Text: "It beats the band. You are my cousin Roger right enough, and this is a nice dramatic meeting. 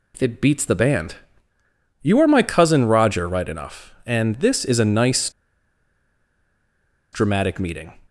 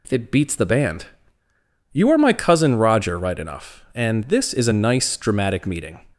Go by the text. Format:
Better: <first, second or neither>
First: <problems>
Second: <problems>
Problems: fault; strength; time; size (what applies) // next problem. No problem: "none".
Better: second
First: pauses between "nice" and "dramatic"; strong; at 5.2 s; 1.8 s long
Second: none